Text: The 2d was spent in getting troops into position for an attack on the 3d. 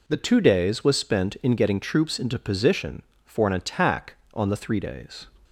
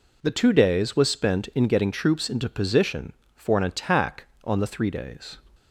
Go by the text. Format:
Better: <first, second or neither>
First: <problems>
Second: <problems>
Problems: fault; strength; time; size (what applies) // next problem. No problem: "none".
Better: neither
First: none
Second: none